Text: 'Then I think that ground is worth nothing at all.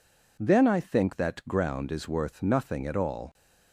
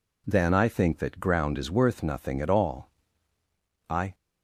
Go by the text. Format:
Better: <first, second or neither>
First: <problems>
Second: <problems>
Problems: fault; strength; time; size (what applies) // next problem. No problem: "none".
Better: first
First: none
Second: goes on to say "I"; slight; from 3.9 s on; 0.24 s long